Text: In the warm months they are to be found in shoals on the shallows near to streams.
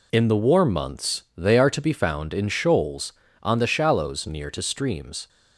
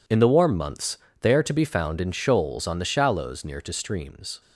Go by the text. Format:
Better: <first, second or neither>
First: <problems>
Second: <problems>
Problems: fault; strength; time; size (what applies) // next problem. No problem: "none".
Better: neither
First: pauses between "months" and "they"; slight; at 1.2 s; 0.16 s long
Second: pauses between "months" and "they"; slight; at 0.9 s; 0.24 s long